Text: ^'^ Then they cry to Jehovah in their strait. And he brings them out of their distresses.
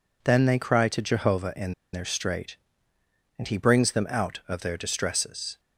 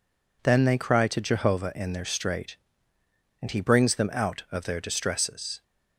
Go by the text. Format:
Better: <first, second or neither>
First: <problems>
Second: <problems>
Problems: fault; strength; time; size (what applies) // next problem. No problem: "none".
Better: second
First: pauses between "in" and "their"; slight; at 1.7 s; 0.20 s long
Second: none